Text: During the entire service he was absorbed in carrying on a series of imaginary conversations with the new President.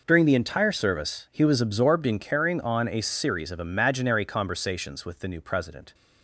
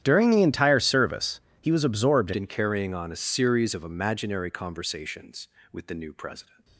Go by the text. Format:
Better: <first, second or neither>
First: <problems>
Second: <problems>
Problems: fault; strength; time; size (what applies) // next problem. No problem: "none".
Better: first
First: none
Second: starts louder than the rest; strong; until 1.0 s; 10.5 dB // pauses between "service" and "he"; slight; at 1.3 s; 0.20 s long // changes voice at "in"; from 2.3 s on; 4.3 s long